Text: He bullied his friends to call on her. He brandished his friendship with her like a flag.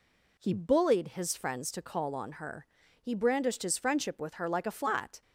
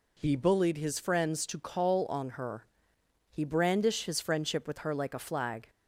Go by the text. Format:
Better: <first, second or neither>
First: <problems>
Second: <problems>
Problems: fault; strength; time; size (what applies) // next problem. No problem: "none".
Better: second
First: says "flat" for "flag"; at 4.7 s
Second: none